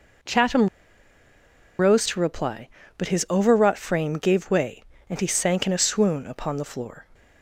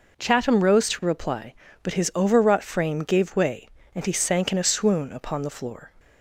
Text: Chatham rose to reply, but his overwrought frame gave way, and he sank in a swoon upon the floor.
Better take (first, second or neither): second